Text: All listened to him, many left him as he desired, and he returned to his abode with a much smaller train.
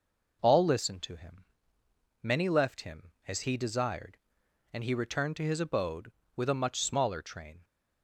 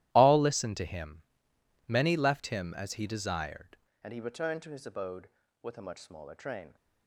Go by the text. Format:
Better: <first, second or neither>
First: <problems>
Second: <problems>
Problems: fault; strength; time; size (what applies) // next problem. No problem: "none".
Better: first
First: none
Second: starts louder than the rest; strong; until 1.1 s; 14.5 dB // changes voice at "and"; from 4.0 s on; 2.7 s long